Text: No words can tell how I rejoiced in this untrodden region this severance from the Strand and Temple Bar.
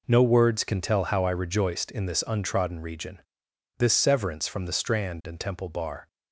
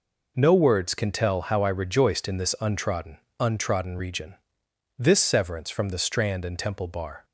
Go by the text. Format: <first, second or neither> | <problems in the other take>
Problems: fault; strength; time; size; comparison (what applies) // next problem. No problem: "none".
first | says "untrodden" twice; at 3.4 s // pauses between "region" and "this"; noticeable; at 4.3 s; 0.64 s long; noticeable in the first